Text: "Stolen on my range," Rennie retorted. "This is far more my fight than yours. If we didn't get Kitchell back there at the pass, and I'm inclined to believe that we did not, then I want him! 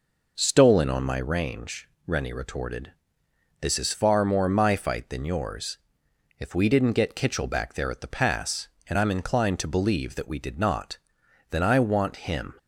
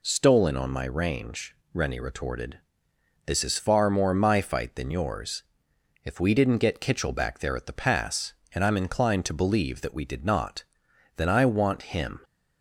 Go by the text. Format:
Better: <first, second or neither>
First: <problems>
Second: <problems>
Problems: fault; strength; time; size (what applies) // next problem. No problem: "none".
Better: second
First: starts louder than the rest; noticeable; until 1.4 s; 5 dB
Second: none